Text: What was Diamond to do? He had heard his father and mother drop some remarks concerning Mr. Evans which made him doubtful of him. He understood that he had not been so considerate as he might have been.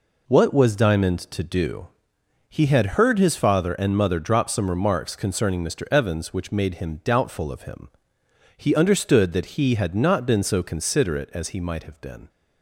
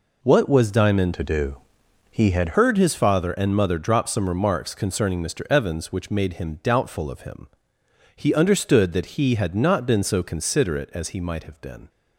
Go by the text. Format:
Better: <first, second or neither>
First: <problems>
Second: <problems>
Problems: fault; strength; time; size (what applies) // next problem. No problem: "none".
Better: first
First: none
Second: changes voice from "to" to "had"; from 1.1 to 2.5 s; 1.4 s long